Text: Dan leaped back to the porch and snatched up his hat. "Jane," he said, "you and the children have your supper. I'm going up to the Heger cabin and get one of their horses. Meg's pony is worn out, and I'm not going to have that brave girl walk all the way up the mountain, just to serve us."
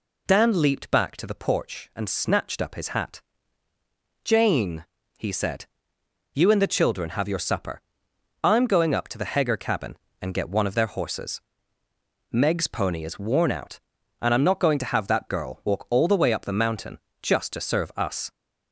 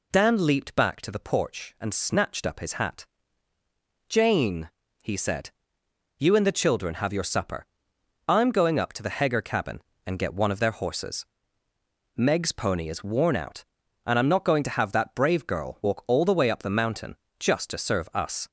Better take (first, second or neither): second